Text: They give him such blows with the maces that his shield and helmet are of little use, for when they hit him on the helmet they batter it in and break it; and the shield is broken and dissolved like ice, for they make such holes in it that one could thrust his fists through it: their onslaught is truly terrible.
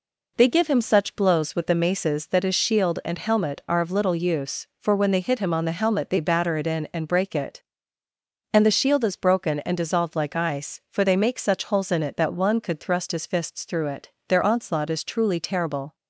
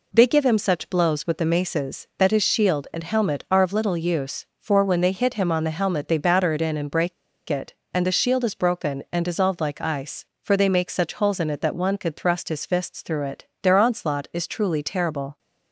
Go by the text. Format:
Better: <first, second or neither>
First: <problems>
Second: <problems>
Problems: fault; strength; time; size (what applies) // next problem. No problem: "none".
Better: first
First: none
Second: pauses between "break" and "it"; at 7.1 s; 0.36 s long